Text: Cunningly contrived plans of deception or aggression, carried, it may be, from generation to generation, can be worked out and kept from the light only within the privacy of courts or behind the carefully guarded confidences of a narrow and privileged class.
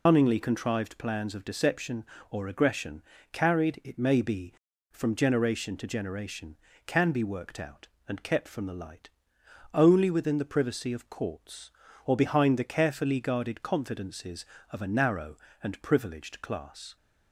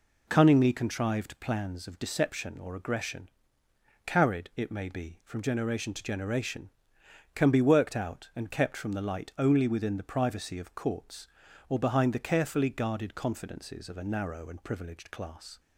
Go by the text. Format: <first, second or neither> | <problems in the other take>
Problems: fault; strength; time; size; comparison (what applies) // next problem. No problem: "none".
second | loses the start of "Cunningly"; at 0.0 s; 135 ms // pauses between "light" and "only"; noticeable; at 9.0 s; 0.64 s long